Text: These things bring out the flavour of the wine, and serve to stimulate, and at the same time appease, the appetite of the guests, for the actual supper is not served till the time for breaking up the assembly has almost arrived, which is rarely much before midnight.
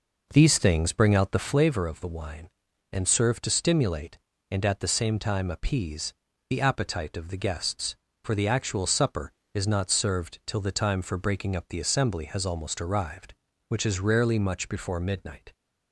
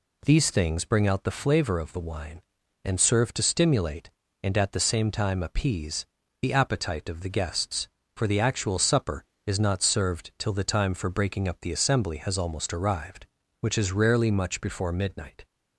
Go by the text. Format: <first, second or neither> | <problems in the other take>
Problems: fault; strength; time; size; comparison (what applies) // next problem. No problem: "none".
second | starts louder than the rest; noticeable; until 1.8 s; 5 dB